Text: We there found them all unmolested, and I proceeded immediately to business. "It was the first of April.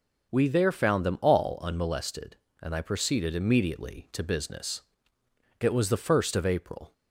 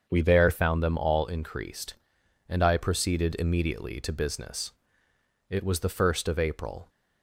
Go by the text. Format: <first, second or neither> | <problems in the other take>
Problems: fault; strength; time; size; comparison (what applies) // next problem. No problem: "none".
first | starts louder than the rest; until 1.0 s; 7 dB; noticeable in the first // says "increased" for "unmolested"; at 1.2 s